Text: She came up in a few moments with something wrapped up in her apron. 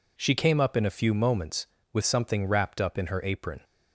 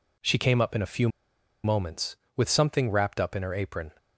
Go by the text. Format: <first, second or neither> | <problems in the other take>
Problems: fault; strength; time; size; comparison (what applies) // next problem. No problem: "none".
first | pauses between "few" and "moments"; noticeable; at 1.0 s; 0.56 s long